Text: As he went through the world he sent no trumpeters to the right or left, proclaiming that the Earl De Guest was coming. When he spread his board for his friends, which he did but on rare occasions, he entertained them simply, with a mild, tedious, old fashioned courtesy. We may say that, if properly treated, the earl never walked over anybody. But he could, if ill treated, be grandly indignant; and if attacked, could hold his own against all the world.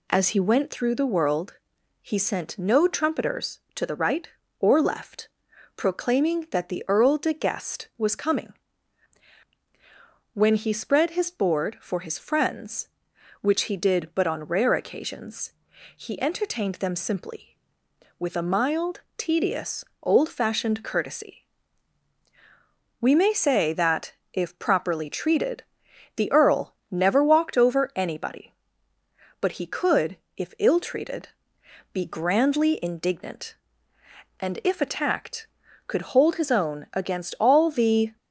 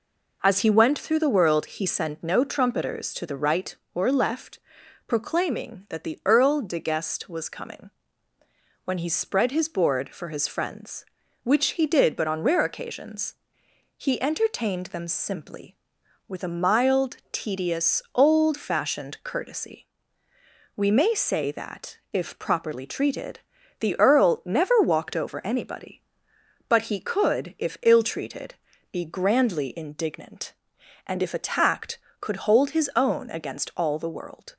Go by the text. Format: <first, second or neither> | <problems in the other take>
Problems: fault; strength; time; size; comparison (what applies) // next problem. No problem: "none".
second | pauses between "world" and "he"; noticeable; at 1.5 s; 0.48 s long // pauses between "earl" and "never"; slight; at 26.7 s; 0.16 s long // stops before "world"; at 38.1 s